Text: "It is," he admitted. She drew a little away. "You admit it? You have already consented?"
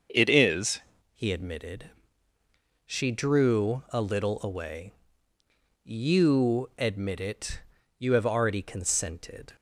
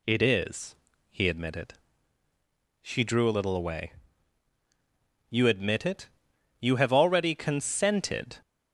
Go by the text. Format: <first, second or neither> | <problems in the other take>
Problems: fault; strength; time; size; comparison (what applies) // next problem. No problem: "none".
second | starts louder than the rest; until 1.4 s; 6.5 dB // changes voice at "he"; from 1.1 s on; 8.4 s long